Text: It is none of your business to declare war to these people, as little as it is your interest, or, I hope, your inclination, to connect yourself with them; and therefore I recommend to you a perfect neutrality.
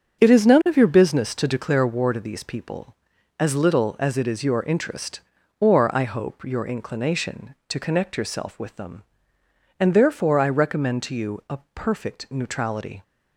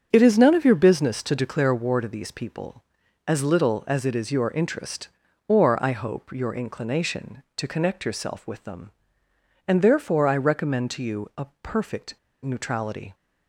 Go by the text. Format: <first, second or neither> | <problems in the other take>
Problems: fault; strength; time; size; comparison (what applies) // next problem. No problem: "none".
first | starts louder than the rest; strong; until 1.1 s; 7 dB; strong in the first // pauses between "a" and "perfect"; slight; at 11.4 s; 0.16 s long; slight in the first // pauses between "perfect" and "neutrality"; slight; at 12.1 s; 0.28 s long